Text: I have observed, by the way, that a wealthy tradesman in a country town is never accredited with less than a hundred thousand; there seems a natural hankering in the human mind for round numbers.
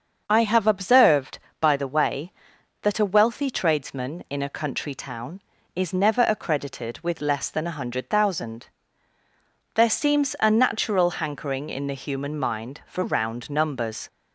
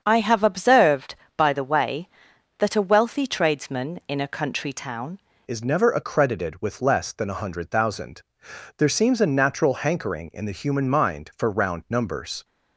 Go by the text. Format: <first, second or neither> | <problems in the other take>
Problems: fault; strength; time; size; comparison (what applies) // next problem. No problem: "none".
first | starts louder than the rest; until 1.0 s; 7 dB; also in the first // changes voice at "is"; from 5.4 s on; 7.0 s long